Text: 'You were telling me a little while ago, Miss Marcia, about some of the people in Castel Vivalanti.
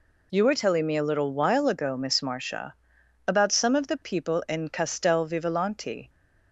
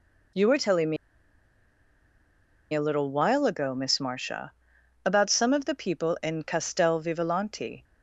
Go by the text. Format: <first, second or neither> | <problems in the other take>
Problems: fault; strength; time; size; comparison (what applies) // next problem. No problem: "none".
first | pauses between "me" and "a"; strong; at 0.9 s; 1.7 s long